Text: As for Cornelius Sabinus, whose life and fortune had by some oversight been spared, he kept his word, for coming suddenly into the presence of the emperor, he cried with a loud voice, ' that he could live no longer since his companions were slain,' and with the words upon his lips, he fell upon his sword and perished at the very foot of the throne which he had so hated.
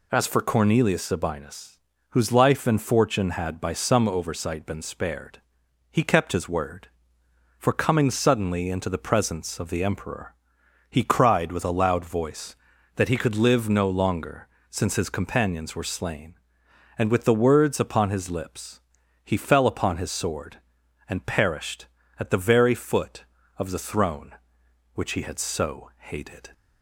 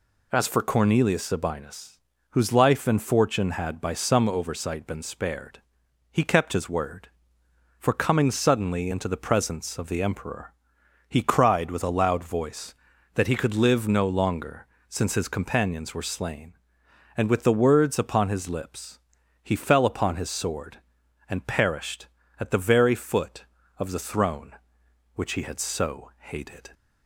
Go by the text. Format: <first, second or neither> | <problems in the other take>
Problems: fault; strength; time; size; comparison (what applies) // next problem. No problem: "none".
neither | pauses between "longer" and "since"; slight; the same in both